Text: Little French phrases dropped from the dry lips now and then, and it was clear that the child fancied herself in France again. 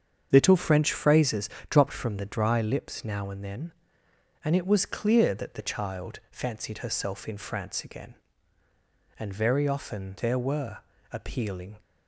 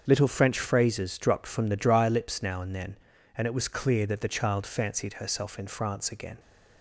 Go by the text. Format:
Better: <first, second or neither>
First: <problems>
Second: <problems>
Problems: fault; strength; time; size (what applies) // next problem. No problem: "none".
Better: second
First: starts louder than the rest; strong; until 1.3 s; 7.5 dB // pauses between "phrases" and "dropped"; slight; at 1.4 s; 0.20 s long // goes on to say "And very often there were appealing"; strong; from 9.1 s on; 2.6 s long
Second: starts louder than the rest; until 1.0 s; 7 dB